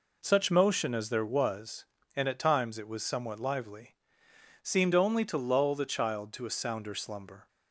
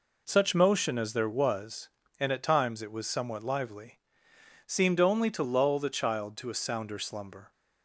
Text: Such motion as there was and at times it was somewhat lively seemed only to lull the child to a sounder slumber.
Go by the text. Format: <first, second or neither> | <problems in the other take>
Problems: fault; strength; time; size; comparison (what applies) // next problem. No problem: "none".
neither | pauses between "lively" and "seemed"; noticeable; the same in both